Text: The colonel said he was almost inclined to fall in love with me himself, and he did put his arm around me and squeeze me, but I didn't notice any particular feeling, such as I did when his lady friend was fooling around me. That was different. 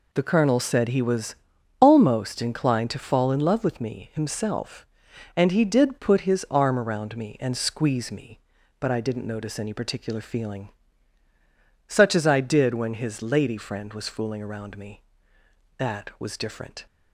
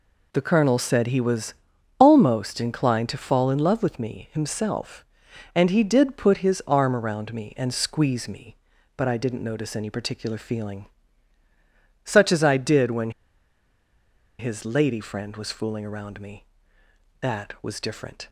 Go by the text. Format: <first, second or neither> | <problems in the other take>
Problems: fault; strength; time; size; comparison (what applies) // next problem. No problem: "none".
first | pauses between "was" and "almost"; at 1.5 s; 0.44 s long; also in the first // pauses between "when" and "his"; strong; at 13.1 s; 1.2 s long